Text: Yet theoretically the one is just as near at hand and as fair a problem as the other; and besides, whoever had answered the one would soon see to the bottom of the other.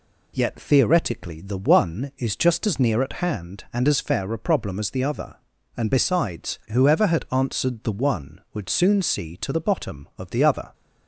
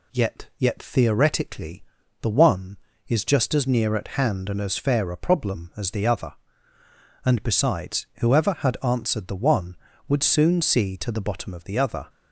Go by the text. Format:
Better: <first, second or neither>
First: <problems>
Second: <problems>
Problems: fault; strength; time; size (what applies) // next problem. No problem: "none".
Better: first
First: none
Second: says "Yet" twice; at 0.5 s // pauses between "theoretically" and "the"; at 1.8 s; 0.38 s long